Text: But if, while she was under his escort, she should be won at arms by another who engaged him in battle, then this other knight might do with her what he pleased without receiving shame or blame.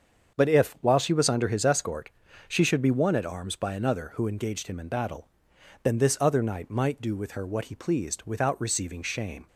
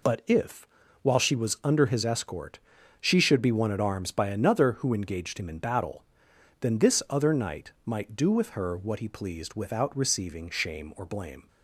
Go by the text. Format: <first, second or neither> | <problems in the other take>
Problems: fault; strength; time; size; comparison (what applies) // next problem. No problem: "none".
second | starts louder than the rest; until 1.4 s; 7 dB // stops before "or blame"; at 9.4 s